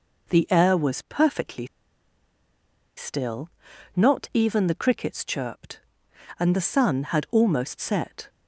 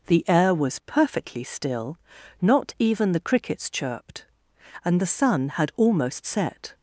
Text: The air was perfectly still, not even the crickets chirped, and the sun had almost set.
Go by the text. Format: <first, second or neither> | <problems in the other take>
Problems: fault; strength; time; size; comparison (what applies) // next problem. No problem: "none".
second | pauses between "perfectly" and "still"; strong; at 1.6 s; 1.3 s long